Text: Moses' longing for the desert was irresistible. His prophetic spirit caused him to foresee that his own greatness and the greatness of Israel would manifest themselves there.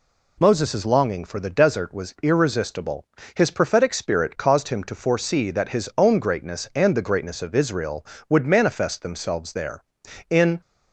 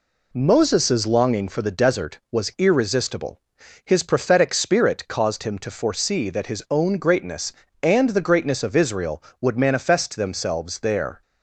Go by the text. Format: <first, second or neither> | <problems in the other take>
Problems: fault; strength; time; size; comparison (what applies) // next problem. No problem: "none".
second | goes on to say "In"; slight; from 10.3 s on; 0.30 s long